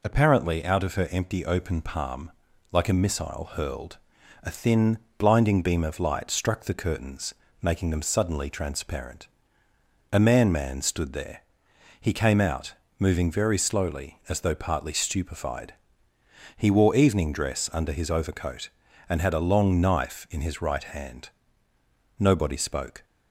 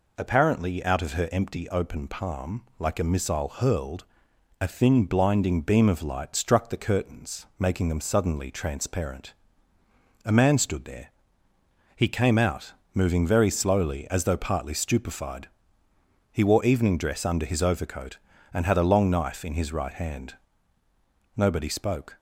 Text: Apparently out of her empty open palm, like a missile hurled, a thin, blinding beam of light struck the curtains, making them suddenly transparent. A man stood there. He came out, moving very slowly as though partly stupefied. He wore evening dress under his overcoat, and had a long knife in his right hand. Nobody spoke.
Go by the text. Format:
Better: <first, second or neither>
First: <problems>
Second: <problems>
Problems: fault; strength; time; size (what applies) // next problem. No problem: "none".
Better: second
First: says "man" twice; at 10.5 s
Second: none